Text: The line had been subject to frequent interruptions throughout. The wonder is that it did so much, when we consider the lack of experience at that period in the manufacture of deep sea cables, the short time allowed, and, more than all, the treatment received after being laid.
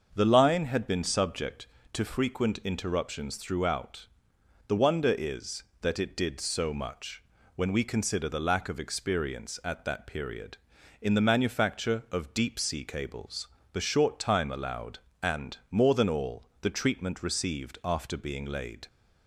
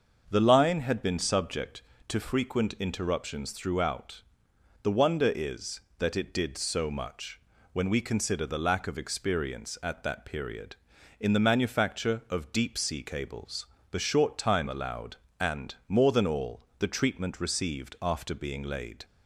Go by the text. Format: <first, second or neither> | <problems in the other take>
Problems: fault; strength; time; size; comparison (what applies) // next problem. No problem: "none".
neither | starts louder than the rest; the same in both